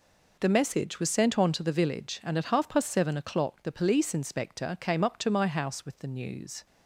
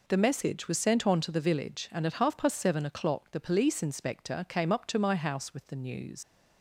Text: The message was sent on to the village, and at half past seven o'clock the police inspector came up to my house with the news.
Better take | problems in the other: first | leaves "news" unfinished; at 6.2 s; 110 ms

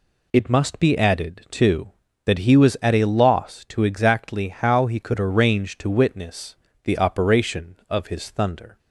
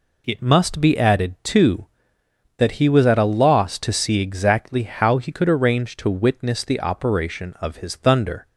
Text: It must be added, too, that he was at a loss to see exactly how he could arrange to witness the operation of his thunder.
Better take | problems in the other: second | skips "see"; at 3.8 s // pauses between "witness" and "the"; slight; at 6.5 s; 0.30 s long

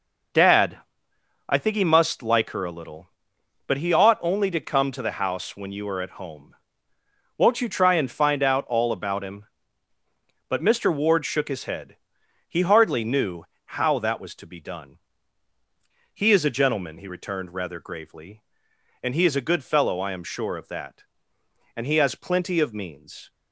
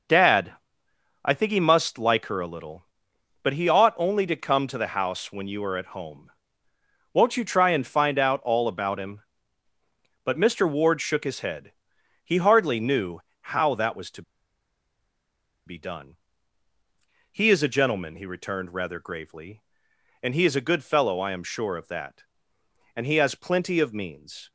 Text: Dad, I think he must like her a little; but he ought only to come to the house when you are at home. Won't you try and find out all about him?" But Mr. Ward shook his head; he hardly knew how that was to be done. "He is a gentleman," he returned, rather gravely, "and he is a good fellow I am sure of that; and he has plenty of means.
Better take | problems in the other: first | pauses between "knew" and "how"; slight; at 13.1 s; 0.22 s long; slight in the first // pauses between "to" and "be"; strong; at 14.2 s; 1.4 s long

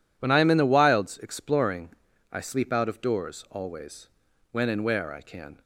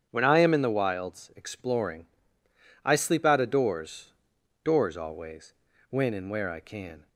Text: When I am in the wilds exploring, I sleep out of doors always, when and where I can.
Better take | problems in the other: first | starts louder than the rest; strong; until 1.1 s; 8.5 dB // says "doors" twice; at 4.6 s

